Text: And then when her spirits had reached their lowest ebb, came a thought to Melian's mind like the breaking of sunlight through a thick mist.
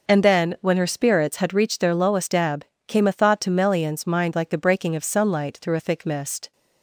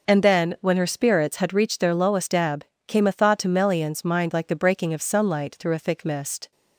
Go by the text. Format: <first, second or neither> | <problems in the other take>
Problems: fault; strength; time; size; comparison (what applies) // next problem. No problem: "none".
neither | none